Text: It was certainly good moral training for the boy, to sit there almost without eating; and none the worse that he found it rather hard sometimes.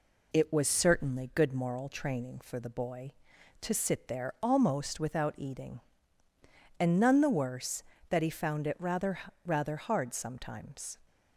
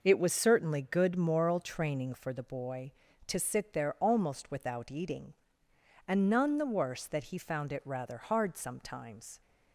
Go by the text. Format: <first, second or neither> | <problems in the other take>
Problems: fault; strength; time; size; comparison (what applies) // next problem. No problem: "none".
second | says "rather" twice; at 9.4 s